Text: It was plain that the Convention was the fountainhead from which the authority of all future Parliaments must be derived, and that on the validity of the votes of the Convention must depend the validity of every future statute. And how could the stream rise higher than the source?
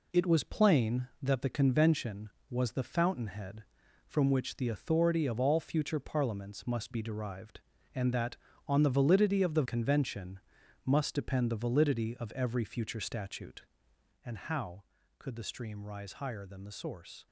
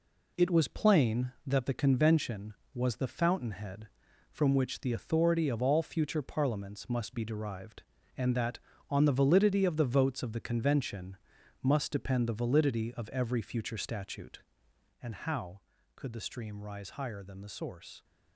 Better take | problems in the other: second | skips "votes of the"; at 9.6 s // pauses between "Convention" and "must"; noticeable; at 10.3 s; 0.48 s long; noticeable in the second

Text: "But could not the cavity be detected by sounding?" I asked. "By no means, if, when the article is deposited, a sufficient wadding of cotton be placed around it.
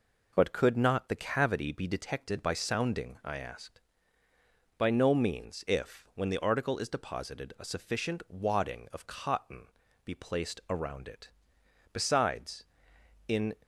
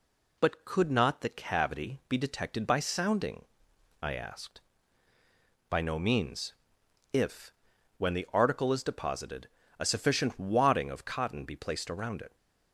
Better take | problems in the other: second | pauses between "cotton" and "be"; at 9.6 s; 0.38 s long // goes on to say "Besides in"; from 11.9 s on; 1.6 s long

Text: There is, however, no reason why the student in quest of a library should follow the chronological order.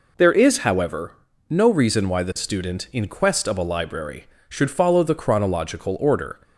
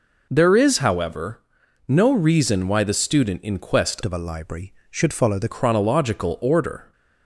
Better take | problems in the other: first | changes voice from "of" to "the"; from 4.0 to 5.4 s; 1.4 s long

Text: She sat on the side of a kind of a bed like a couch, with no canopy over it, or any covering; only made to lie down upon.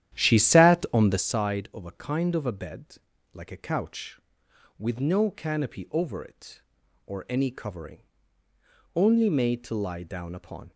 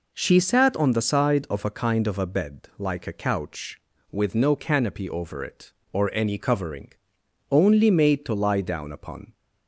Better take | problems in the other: second | starts louder than the rest; strong; until 1.4 s; 11 dB // pauses between "bed" and "like"; slight; at 2.9 s; 0.36 s long

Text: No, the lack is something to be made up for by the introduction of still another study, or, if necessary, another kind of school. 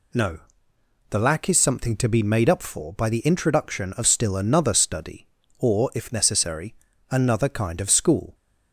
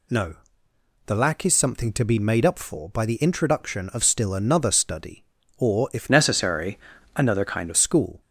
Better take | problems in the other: first | changes voice from "necessary" to "of"; from 6.0 to 7.7 s; 1.7 s long

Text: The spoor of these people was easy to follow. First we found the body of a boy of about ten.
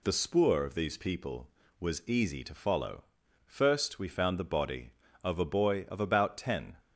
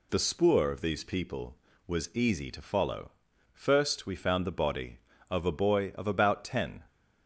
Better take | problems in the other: neither | none

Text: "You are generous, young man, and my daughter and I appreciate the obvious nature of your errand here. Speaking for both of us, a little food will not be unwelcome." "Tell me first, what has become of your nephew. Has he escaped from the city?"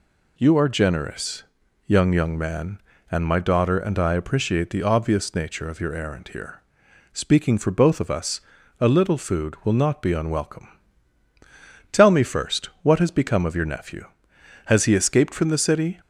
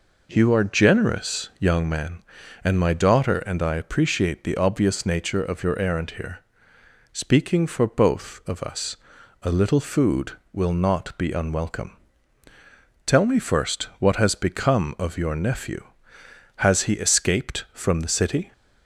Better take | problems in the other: second | says "young" twice; at 2.1 s

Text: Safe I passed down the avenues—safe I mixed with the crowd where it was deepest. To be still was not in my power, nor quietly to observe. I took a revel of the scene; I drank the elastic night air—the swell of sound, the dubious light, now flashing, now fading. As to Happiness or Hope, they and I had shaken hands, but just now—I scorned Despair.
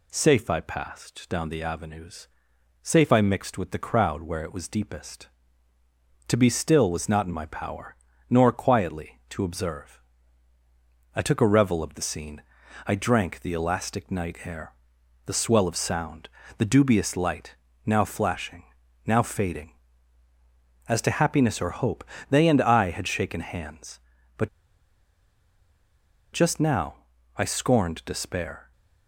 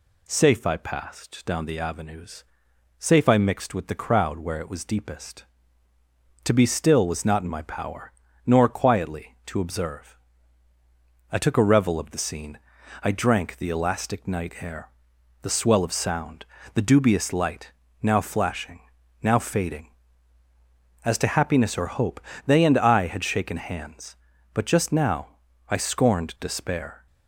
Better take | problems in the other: second | pauses between "but" and "just"; strong; at 24.4 s; 1.8 s long

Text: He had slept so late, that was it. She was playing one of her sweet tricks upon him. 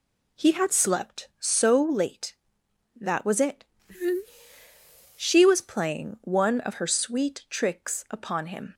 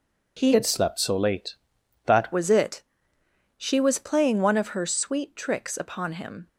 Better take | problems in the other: first | changes voice from "had" to "that"; from 0.5 to 2.3 s; 1.8 s long

